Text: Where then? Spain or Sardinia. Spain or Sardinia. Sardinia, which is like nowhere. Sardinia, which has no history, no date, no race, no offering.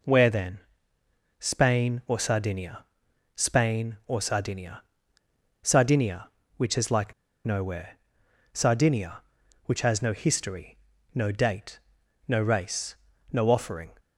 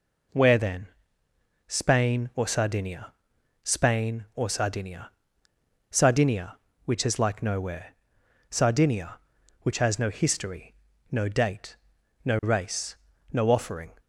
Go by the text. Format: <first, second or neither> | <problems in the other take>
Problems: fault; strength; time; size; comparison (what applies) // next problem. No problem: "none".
second | pauses between "like" and "nowhere"; slight; at 7.1 s; 0.31 s long